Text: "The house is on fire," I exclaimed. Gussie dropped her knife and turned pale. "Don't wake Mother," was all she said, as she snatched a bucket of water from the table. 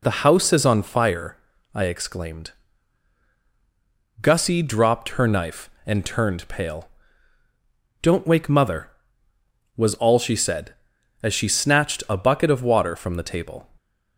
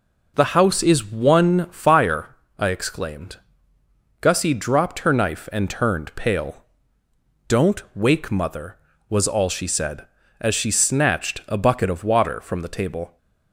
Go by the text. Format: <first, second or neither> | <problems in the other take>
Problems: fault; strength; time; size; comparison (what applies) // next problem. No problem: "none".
first | says "one" for "on"; at 1.0 s